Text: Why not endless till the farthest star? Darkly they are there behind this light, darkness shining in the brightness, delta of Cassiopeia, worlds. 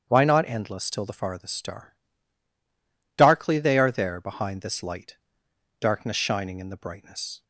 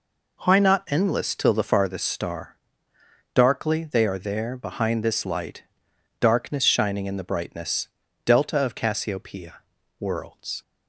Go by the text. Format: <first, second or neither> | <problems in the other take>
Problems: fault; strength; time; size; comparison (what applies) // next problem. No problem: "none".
second | starts louder than the rest; strong; until 1.0 s; 7.5 dB // stops before "delta of Cassiopeia worlds"; at 7.4 s